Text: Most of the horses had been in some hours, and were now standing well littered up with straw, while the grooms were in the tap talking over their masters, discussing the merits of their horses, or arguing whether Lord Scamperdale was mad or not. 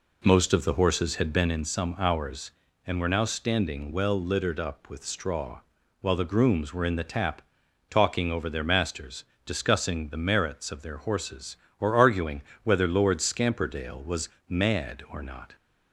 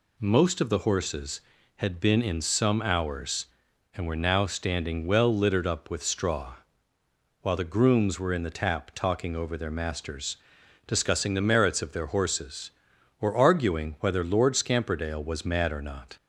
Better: second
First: starts louder than the rest; slight; until 1.5 s; 3.5 dB // pauses between "tap" and "talking"; noticeable; at 7.4 s; 0.48 s long // pauses between "arguing" and "whether"; slight; at 12.4 s; 0.20 s long // pauses between "was" and "mad"; slight; at 14.2 s; 0.18 s long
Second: none

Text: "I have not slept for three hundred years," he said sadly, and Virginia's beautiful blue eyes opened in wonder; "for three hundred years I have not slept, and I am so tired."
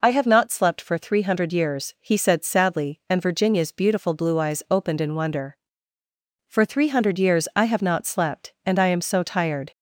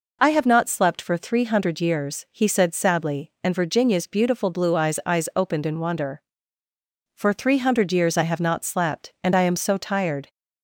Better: first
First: none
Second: says "eyes" twice; at 5.0 s

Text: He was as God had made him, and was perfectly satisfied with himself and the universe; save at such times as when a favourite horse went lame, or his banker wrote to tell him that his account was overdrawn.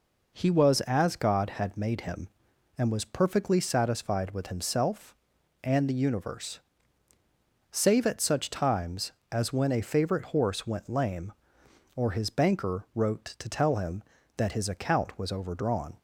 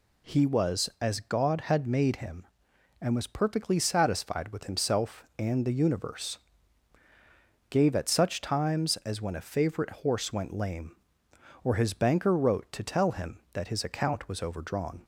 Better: first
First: none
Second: says "gave" for "save"; at 7.6 s

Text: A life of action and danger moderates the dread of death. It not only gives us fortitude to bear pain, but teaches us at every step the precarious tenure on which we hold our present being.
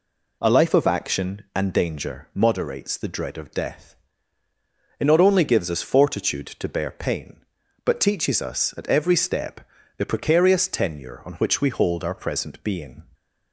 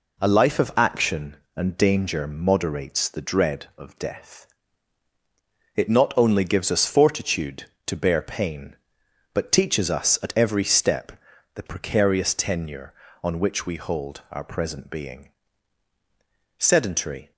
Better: first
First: pauses between "step" and "the"; slight; at 9.6 s; 0.36 s long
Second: pauses between "step" and "the"; at 11.1 s; 0.44 s long // goes on to say "Sedentary"; noticeable; from 16.5 s on; 0.74 s long

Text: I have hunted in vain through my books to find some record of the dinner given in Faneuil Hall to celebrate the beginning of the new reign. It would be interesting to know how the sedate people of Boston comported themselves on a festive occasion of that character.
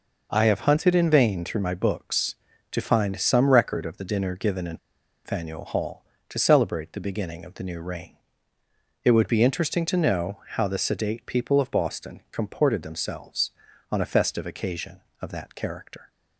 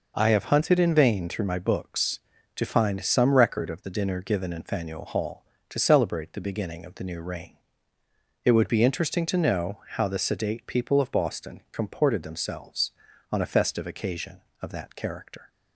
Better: second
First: pauses between "in" and "Faneuil"; noticeable; at 4.7 s; 0.47 s long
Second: none

